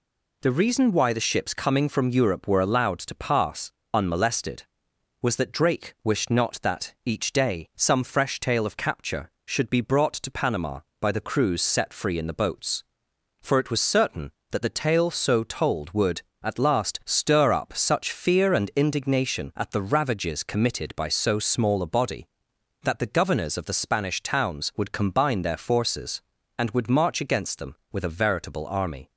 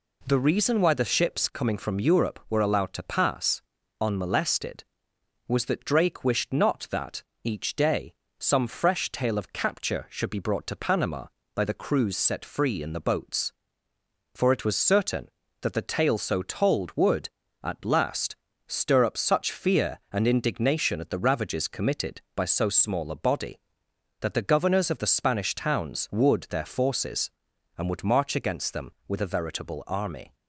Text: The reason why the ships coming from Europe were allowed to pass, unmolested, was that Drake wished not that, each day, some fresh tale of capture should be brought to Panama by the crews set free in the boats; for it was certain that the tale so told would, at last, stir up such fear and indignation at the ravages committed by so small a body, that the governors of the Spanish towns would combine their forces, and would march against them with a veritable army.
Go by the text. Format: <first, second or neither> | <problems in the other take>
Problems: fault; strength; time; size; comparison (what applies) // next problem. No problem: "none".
first | skips "combine"; at 26.4 s